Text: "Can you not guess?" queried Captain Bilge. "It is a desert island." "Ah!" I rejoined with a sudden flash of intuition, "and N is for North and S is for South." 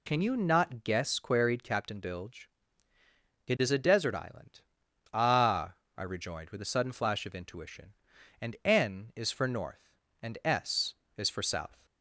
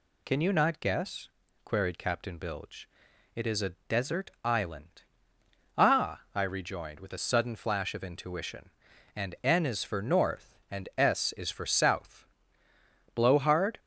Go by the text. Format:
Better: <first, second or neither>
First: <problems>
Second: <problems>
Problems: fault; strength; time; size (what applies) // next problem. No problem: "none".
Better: first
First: none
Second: goes on to say "Blowhard"; noticeable; from 13.1 s on; 0.64 s long